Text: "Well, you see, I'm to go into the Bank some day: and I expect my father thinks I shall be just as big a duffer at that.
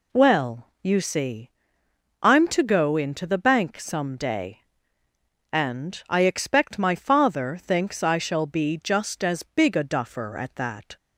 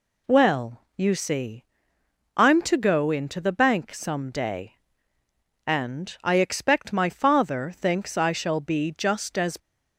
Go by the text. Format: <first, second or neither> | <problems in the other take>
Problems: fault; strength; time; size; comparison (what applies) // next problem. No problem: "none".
first | stops before "big a duffer at that"; at 9.5 s